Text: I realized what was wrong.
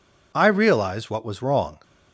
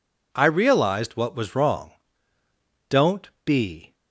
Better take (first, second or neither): first